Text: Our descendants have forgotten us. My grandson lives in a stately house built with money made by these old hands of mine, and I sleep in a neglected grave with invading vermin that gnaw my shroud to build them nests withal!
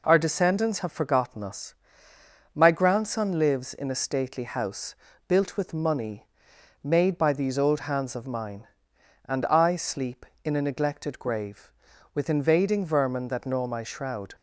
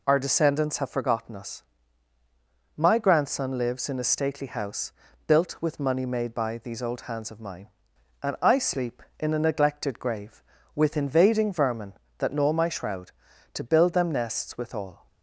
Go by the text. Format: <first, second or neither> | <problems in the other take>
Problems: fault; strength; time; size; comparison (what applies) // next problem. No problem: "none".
second | pauses between "house" and "built"; slight; at 4.9 s; 0.32 s long; slight in the second // pauses between "money" and "made"; noticeable; at 6.2 s; 0.56 s long // stops before "to build them nests withal"; at 14.3 s